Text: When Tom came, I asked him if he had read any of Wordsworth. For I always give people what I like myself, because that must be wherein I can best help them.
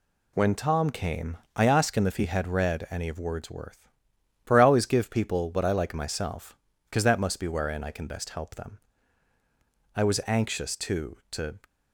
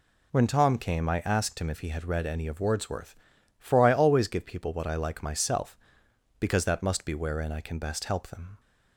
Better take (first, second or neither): second